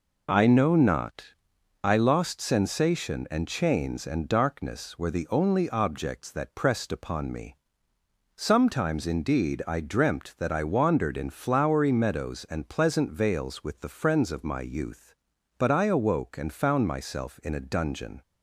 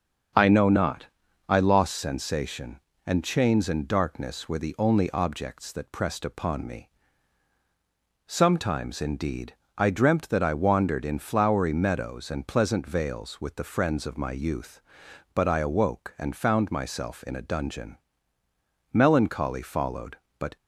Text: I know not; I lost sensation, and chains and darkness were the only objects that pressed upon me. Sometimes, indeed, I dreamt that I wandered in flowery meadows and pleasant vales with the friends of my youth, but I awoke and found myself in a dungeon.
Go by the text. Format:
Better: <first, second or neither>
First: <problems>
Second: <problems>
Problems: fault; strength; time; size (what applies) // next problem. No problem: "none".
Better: first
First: none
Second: starts louder than the rest; until 1.7 s; 7 dB // goes on to say "Melancholy followed but"; from 18.9 s on; 1.6 s long